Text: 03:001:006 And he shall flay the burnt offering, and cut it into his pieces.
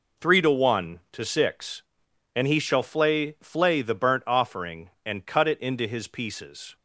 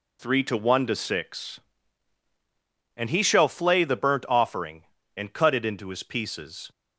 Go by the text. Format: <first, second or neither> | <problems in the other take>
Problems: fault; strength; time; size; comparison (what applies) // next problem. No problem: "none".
second | says "flay" twice; at 3.4 s